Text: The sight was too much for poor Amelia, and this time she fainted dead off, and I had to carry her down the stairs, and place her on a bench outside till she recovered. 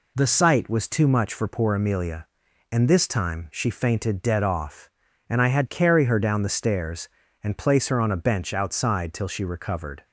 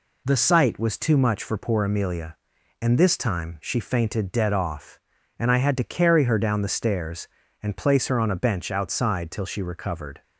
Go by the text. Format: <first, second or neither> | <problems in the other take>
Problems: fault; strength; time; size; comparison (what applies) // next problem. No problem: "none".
second | skips "to"; at 5.6 s